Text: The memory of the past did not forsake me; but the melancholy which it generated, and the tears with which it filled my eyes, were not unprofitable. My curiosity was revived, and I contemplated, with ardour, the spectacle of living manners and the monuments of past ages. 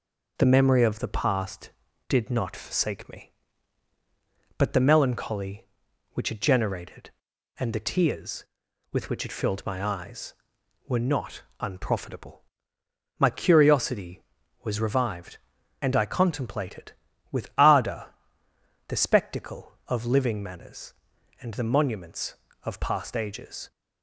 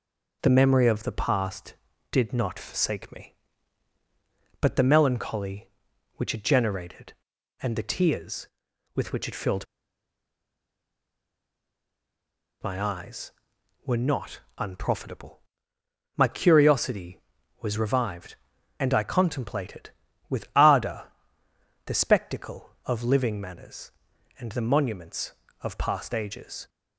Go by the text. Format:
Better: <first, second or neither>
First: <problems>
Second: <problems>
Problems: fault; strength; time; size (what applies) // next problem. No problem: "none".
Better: first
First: pauses between "not" and "unprofitable"; slight; at 11.4 s; 0.18 s long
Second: pauses between "filled" and "my"; strong; at 9.6 s; 2.9 s long // pauses between "not" and "unprofitable"; slight; at 14.3 s; 0.18 s long